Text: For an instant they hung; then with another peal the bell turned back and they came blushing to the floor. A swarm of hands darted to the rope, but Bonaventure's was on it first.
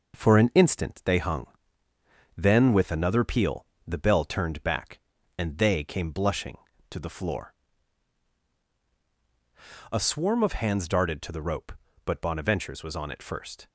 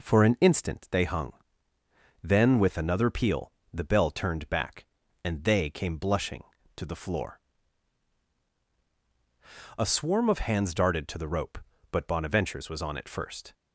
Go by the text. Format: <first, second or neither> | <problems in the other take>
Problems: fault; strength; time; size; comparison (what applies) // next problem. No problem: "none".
second | gets quieter; noticeable; throughout; 4.5 dB // pauses between "peal" and "the"; slight; at 3.6 s; 0.20 s long; slight in the second